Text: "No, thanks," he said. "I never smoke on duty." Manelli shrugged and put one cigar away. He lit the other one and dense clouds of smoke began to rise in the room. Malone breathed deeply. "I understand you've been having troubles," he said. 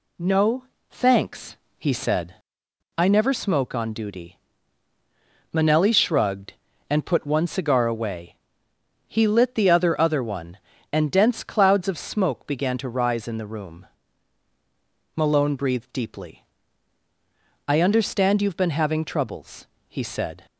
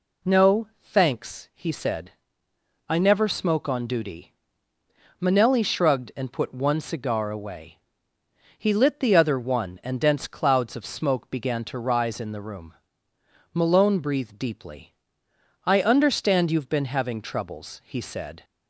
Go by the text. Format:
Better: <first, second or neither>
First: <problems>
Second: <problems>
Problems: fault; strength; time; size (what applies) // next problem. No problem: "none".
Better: second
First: says "other" twice; at 9.9 s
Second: none